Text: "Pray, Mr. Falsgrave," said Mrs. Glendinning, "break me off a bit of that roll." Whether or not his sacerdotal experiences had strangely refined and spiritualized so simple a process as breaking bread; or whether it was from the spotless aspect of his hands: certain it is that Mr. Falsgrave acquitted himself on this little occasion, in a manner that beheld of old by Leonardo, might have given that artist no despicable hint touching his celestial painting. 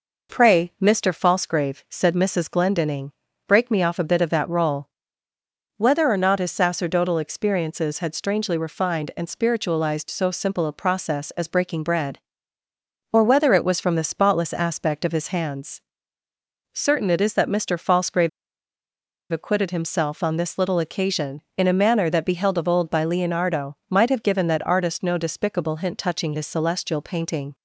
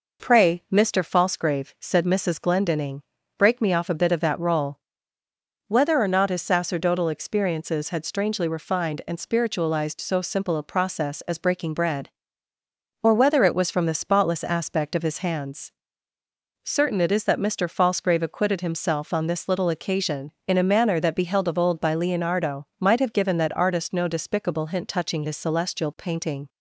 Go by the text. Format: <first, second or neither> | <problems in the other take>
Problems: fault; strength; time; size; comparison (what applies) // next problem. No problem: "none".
second | pauses between "Falsgrave" and "acquitted"; at 18.2 s; 1.0 s long